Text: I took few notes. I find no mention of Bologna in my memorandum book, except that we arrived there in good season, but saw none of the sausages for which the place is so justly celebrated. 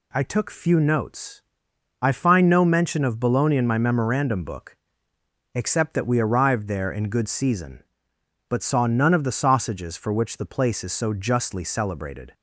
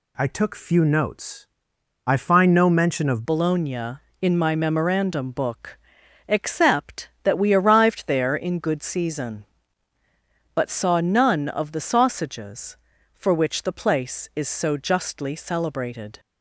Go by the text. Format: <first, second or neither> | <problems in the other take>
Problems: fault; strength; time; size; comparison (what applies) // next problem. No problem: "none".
first | changes voice at "Bologna"; from 3.2 s on; 12.9 s long